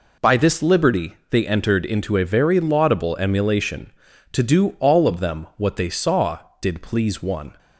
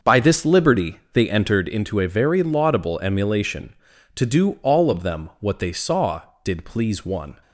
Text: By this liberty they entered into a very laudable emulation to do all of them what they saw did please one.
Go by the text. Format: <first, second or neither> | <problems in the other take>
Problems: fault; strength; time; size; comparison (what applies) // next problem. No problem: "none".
first | starts louder than the rest; until 1.6 s; 6 dB